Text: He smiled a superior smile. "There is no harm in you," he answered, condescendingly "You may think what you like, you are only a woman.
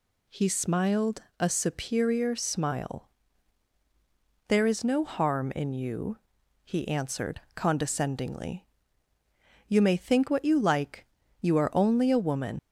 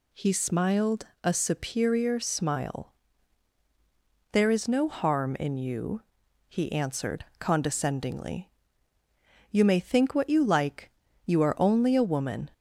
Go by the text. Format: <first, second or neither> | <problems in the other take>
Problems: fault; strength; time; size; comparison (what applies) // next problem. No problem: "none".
second | pauses between "smiled" and "a"; slight; at 1.2 s; 0.18 s long; slight in the second // pauses between "condescendingly" and "You"; at 8.6 s; 1.0 s long; also in the second // leaves "woman" unfinished; at 12.5 s; 90 ms